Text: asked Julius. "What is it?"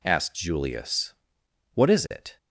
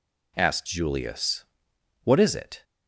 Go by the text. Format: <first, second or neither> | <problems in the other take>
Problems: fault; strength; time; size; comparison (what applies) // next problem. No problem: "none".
neither | none